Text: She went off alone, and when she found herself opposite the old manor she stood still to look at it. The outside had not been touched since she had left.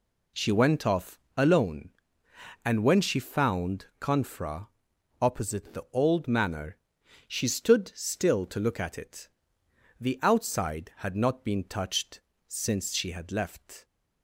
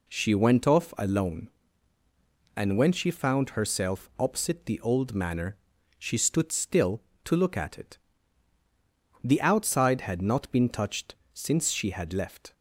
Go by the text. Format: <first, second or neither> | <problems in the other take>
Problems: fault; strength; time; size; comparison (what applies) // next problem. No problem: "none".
second | pauses between "off" and "alone"; slight; at 1.1 s; 0.18 s long // says "confra" for "herself"; at 3.9 s // pauses between "manor" and "she"; noticeable; at 6.7 s; 0.52 s long; also in the second // pauses between "touched" and "since"; slight; at 12.1 s; 0.28 s long; slight in the second